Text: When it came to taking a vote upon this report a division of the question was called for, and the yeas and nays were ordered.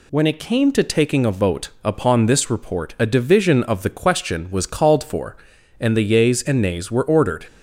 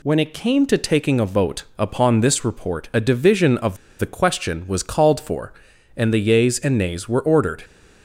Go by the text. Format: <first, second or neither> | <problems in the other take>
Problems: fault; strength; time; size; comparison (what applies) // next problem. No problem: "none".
first | pauses between "of" and "the"; slight; at 3.7 s; 0.23 s long